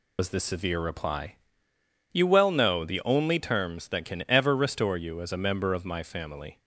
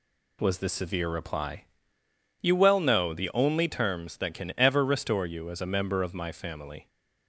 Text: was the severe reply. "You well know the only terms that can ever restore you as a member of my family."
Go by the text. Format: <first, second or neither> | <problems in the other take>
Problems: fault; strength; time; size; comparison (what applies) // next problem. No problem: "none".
second | loses the start of "was"; at 0.1 s; 90 ms